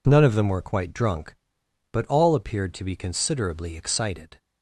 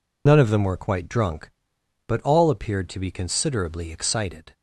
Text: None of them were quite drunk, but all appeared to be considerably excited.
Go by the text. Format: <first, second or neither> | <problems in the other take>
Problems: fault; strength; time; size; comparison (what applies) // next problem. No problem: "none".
first | loses the start of "None"; at 0.2 s; 55 ms